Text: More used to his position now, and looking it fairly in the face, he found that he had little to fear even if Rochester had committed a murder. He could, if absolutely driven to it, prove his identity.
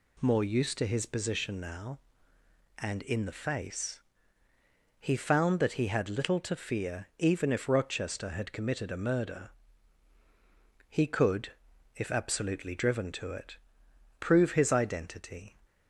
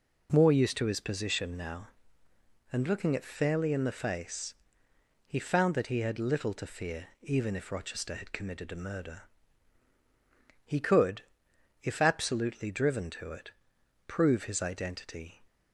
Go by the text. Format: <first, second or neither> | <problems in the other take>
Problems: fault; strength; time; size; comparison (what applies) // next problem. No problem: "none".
second | skips "looking it fairly"; at 3.0 s